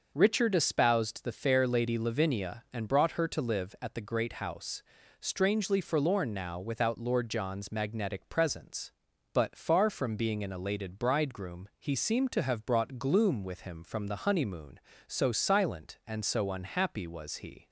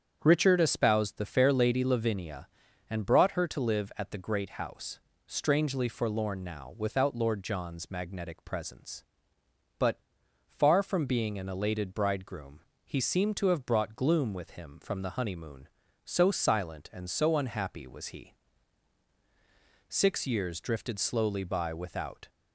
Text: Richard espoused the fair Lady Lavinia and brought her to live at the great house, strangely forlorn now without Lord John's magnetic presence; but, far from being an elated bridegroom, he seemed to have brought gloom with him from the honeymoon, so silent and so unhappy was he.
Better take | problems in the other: first | starts louder than the rest; strong; until 1.2 s; 8 dB // goes on to say "Six years drifted slowly by without"; strong; from 19.8 s on; 2.4 s long

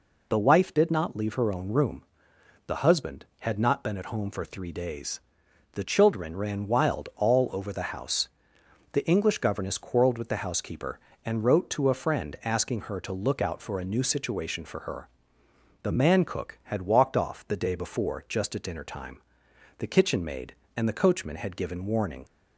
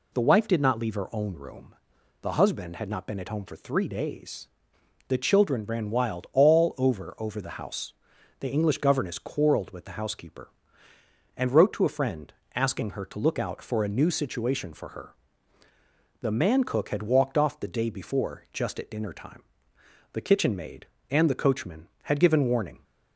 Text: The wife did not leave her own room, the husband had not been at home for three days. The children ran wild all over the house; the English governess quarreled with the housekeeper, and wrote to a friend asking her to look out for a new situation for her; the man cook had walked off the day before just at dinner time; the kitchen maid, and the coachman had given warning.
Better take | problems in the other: first | says "over" twice; at 7.1 s // pauses between "friend" and "asking"; slight; at 12.3 s; 0.22 s long

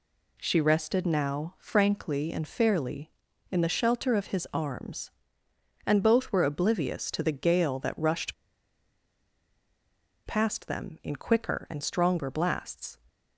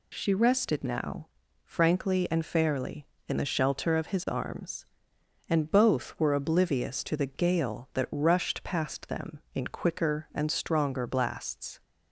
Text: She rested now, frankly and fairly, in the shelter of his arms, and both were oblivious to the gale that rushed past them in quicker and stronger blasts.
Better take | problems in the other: second | pauses between "rushed" and "past"; strong; at 8.3 s; 1.9 s long

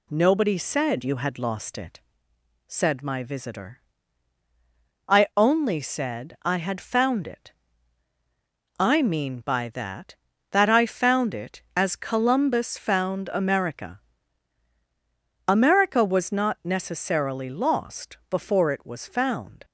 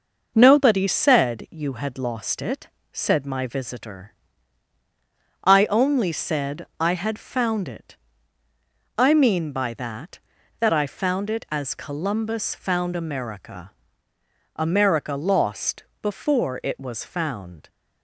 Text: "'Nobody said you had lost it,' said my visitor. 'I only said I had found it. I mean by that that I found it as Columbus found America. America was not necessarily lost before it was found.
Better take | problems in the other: first | skips "was not necessarily"; at 15.1 s // pauses between "lost" and "before"; slight; at 15.8 s; 0.18 s long

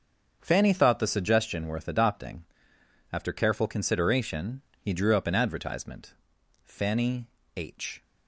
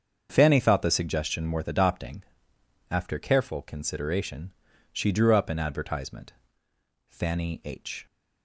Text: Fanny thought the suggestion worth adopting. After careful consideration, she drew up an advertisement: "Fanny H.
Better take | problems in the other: second | starts louder than the rest; until 1.4 s; 7 dB; also in the second // says "he" for "she"; at 4.7 s // pauses between "Fanny" and "H"; slight; at 7.2 s; 0.30 s long

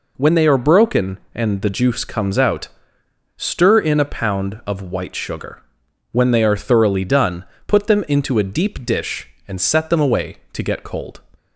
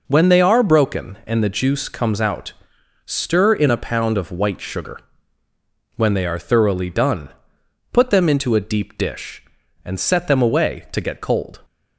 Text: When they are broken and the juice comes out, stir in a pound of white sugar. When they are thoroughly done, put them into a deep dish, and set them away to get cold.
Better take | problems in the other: neither | none

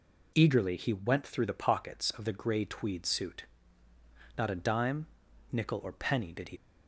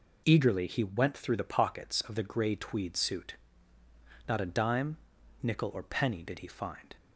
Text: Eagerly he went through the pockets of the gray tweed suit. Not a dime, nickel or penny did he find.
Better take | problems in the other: second | stops before "find"; at 6.5 s

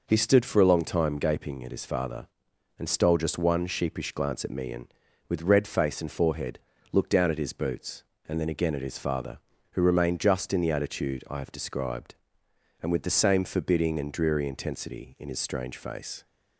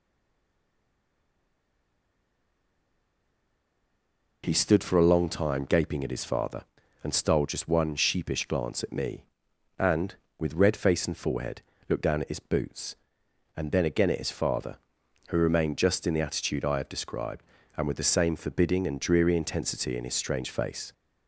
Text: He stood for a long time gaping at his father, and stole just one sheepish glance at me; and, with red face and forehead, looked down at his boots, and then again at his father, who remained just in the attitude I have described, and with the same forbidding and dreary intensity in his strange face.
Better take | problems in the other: first | stays silent before the first word; strong; until 4.4 s; 4.4 s long

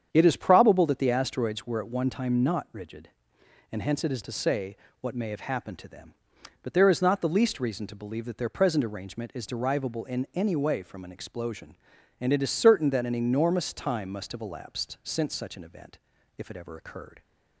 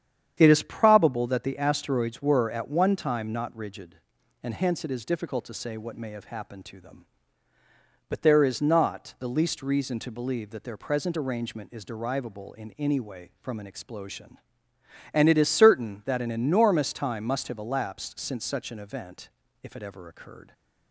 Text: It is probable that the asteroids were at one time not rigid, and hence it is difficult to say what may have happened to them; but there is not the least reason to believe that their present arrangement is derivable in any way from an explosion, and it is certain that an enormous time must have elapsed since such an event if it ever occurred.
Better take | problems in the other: second | starts louder than the rest; strong; until 1.1 s; 8 dB; strong in the second // skips "difficult"; at 4.2 s // pauses between "say" and "what"; slight; at 4.7 s; 0.24 s long // pauses between "event" and "if"; at 15.9 s; 0.40 s long; slight in the second

